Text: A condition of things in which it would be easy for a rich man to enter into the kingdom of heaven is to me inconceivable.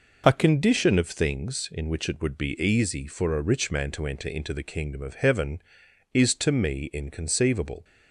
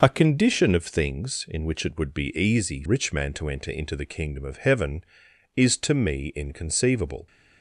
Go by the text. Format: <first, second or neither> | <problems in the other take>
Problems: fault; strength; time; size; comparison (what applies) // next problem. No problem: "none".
first | skips "for a"; at 2.8 s